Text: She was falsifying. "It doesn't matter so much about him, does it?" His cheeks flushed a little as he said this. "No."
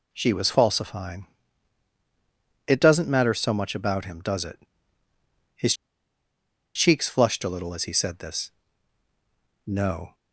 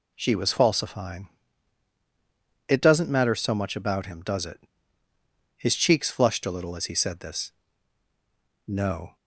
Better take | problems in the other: second | pauses between "His" and "cheeks"; at 5.7 s; 1.0 s long

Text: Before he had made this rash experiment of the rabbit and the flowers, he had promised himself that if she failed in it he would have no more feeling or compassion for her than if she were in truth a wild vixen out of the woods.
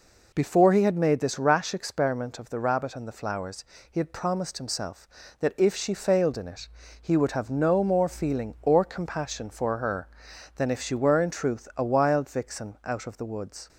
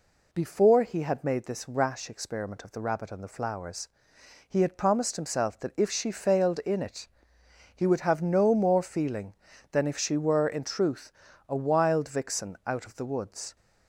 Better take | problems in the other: first | pauses between "it" and "he"; noticeable; at 7.0 s; 0.68 s long; slight in the first // skips "or compassion for her"; at 9.5 s // pauses between "truth" and "a"; at 11.1 s; 0.38 s long

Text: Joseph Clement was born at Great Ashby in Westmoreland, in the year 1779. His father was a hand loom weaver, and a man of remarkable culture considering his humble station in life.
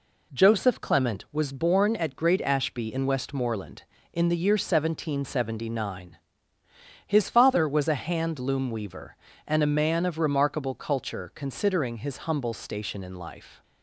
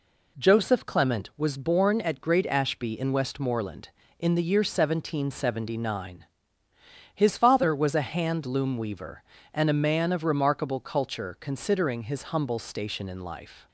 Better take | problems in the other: neither | none

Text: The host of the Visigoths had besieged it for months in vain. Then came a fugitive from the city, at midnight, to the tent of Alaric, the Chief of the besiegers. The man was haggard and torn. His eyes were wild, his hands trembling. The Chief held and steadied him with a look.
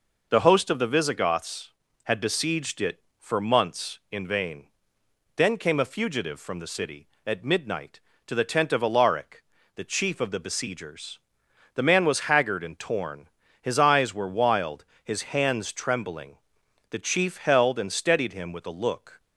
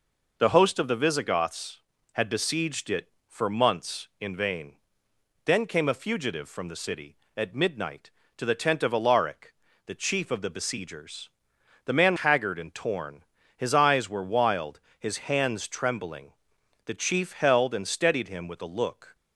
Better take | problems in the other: first | skips "was"; at 12.1 s

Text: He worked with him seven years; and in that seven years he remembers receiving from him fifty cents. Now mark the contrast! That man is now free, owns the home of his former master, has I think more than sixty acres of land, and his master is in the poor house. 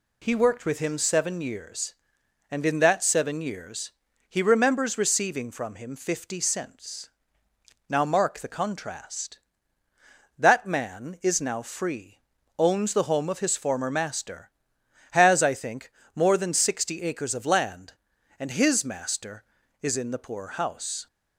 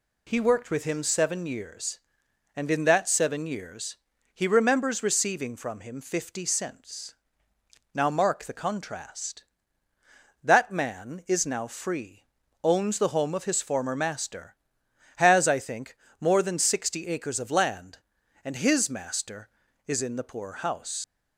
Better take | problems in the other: first | pauses between "years" and "he"; at 3.9 s; 0.38 s long; also in the first // pauses between "think" and "more"; slight; at 15.9 s; 0.24 s long; slight in the first // leaves "house" unfinished; at 21.0 s; 75 ms

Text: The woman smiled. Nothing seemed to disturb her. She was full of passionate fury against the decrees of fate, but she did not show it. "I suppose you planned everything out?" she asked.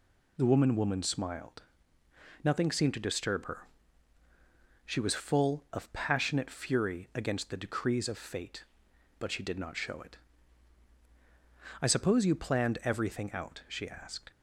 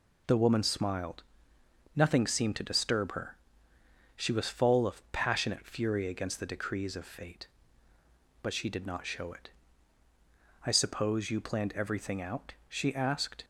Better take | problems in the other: second | says "woman" twice; at 0.7 s

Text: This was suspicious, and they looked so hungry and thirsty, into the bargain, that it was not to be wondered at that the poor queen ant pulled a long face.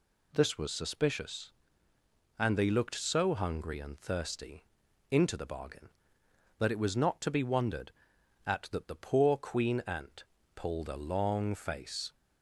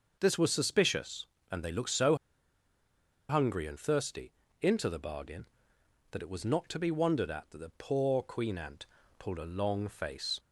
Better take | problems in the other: first | pauses between "so" and "hungry"; at 2.1 s; 1.1 s long // pauses between "ant" and "pulled"; slight; at 8.8 s; 0.32 s long; slight in the first

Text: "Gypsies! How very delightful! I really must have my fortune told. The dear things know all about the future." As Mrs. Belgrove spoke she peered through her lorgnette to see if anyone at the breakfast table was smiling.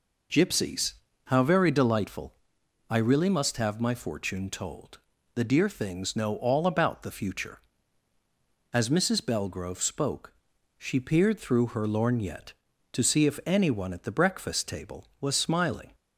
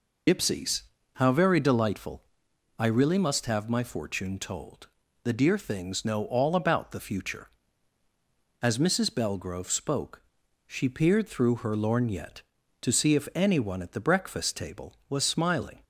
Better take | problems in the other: first | loses the start of "Gypsies"; at 0.2 s; 85 ms // pauses between "spoke" and "she"; at 10.2 s; 0.44 s long; also in the first

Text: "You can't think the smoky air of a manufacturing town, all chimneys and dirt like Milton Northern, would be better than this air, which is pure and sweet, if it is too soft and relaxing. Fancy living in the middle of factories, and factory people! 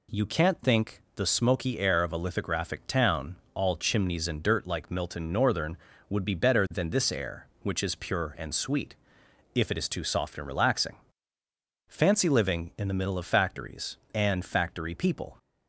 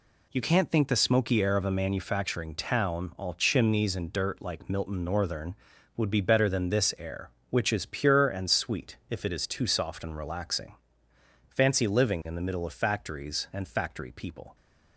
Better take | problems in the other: second | says "lithographic" for "manufacturing"; at 2.1 s

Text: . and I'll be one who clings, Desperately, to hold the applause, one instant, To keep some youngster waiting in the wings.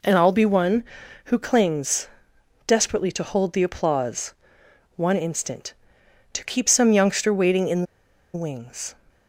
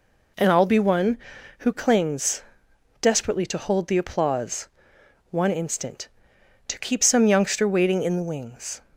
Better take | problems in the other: second | pauses between "in" and "the"; noticeable; at 7.8 s; 0.50 s long

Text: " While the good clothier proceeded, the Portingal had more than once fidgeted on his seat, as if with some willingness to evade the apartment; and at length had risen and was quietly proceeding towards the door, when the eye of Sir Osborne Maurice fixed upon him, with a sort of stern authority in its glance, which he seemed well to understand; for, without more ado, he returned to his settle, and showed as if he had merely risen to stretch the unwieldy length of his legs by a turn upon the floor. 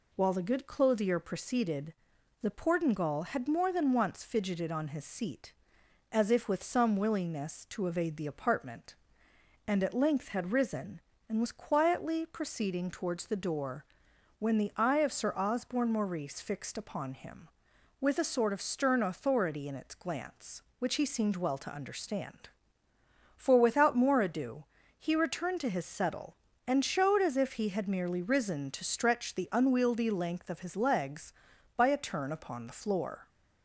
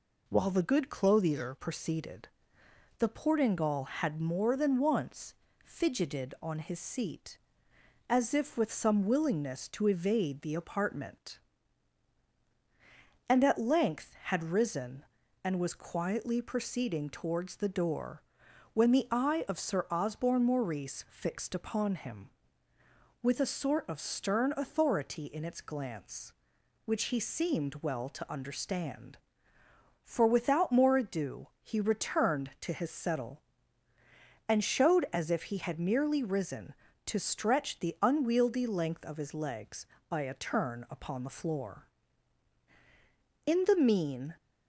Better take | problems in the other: first | pauses between "once" and "fidgeted"; slight; at 5.3 s; 0.30 s long // goes on to say "In the mean"; noticeable; from 43.4 s on; 0.90 s long

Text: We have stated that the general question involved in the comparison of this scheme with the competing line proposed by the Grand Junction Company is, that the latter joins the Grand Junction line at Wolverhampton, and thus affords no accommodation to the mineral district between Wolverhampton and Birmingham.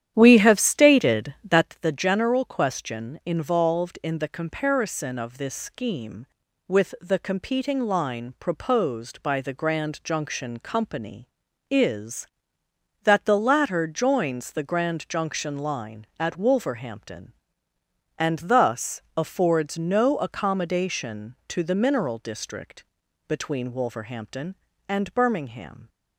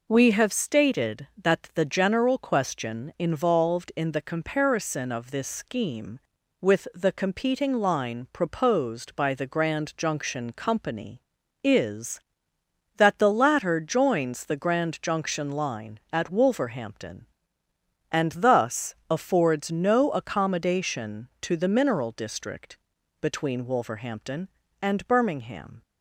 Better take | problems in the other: second | starts louder than the rest; strong; until 1.7 s; 10.5 dB // pauses between "district" and "between"; at 22.8 s; 0.42 s long; also in the second

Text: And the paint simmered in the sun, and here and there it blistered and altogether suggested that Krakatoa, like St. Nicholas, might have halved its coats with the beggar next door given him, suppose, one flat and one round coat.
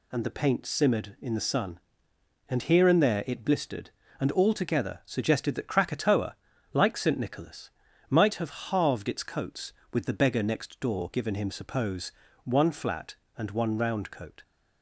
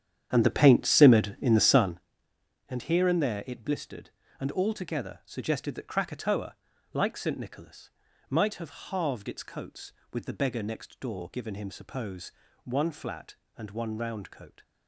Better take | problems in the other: first | starts louder than the rest; strong; until 2.1 s; 9 dB

